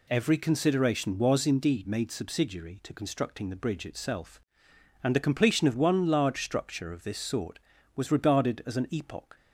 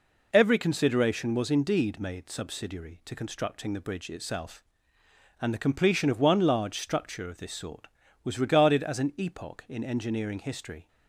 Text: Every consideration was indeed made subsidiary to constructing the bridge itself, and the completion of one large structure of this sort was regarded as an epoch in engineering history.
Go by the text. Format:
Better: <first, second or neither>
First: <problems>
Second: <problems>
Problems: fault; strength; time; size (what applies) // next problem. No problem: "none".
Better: second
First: stops before "in engineering history"; at 9.3 s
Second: none